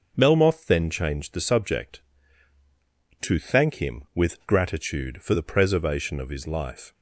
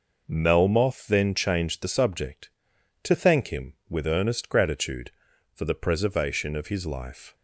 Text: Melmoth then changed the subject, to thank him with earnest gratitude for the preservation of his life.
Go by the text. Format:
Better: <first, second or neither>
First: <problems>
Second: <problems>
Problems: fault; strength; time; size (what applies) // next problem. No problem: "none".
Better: second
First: starts louder than the rest; until 1.1 s; 6 dB // skips "earnest"; at 4.4 s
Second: none